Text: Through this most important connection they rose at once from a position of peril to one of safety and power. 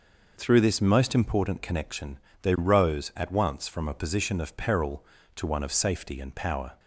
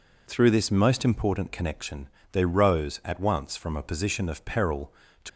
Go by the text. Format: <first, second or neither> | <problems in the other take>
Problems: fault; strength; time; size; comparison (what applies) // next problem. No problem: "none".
first | pauses between "connection" and "they"; slight; at 2.0 s; 0.22 s long; slight in the first // stops before "one of safety and power"; at 5.2 s